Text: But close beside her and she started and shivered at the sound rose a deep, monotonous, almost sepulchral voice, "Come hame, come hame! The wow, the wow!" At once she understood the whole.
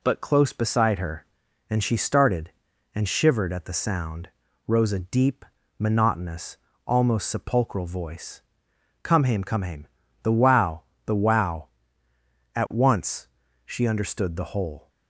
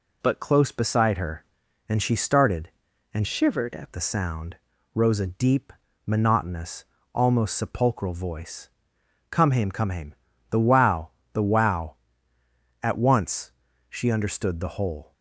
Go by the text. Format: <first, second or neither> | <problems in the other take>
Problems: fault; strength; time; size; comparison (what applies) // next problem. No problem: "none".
first | changes voice from "shivered" to "at"; from 3.2 to 3.9 s; 0.7 s long // pauses between "sound" and "rose"; at 4.5 s; 0.38 s long; also in the first // pauses between "once" and "she"; at 13.5 s; 0.38 s long; also in the first